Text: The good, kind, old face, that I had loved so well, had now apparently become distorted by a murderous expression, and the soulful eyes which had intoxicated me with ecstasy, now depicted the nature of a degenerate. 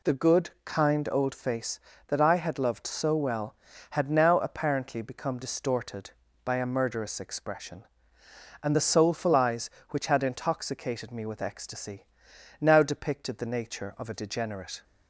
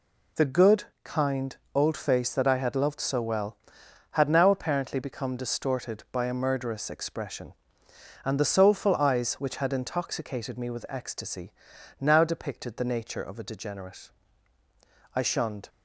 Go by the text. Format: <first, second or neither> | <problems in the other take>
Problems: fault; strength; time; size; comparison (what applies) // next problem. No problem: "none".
first | goes on to say "I shunned"; from 15.1 s on; 0.54 s long